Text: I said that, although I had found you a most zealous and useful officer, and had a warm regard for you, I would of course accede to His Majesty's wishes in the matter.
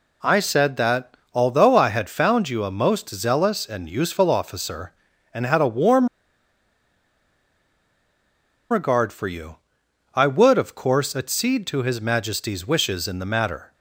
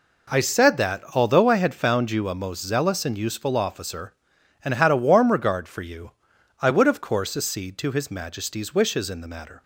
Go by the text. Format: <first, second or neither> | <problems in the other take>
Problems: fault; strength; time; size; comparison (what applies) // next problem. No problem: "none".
second | pauses between "warm" and "regard"; strong; at 6.0 s; 2.6 s long